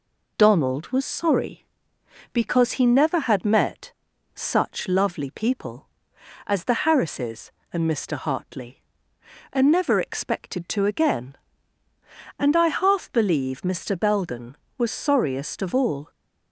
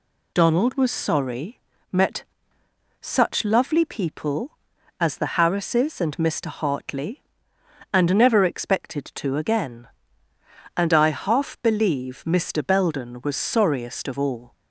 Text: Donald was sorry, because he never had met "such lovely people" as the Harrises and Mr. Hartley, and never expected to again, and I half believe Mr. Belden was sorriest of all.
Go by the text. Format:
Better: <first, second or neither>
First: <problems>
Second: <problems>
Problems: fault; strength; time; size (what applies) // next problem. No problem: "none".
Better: first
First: pauses between "met" and "such"; at 3.9 s; 0.42 s long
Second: skips "because he never had"; at 1.7 s // pauses between "met" and "such"; noticeable; at 2.2 s; 0.78 s long